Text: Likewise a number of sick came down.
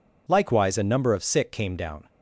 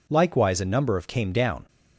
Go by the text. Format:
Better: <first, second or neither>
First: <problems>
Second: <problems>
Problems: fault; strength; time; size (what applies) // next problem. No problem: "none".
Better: first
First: none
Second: skips "sick"; at 1.0 s